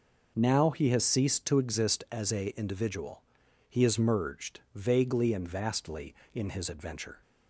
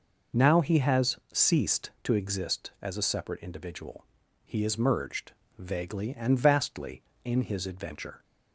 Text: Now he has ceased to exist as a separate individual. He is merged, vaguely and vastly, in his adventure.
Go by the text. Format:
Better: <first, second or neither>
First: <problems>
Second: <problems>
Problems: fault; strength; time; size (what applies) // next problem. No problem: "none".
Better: second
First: skips "separate"; at 2.5 s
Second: none